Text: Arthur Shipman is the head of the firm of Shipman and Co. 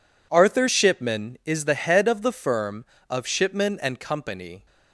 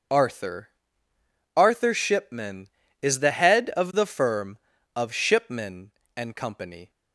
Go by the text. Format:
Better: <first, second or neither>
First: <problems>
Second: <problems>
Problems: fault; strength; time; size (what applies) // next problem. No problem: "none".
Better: first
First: none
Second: says "Arthur" twice; at 1.5 s